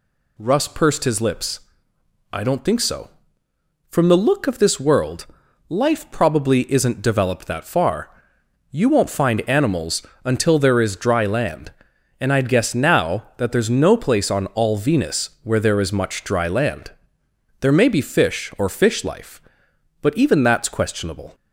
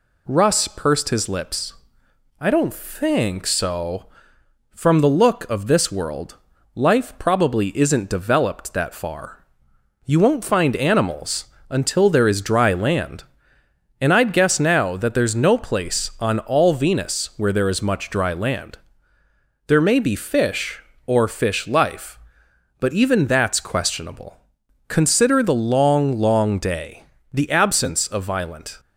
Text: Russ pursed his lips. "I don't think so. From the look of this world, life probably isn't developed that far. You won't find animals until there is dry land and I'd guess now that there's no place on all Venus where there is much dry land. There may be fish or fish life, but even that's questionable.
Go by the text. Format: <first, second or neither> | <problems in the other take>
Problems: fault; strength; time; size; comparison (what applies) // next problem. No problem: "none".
first | pauses between "animals" and "until"; slight; at 11.4 s; 0.24 s long; slight in the first // goes on to say "Consider the long long day the absence of violent"; strong; from 24.8 s on; 3.9 s long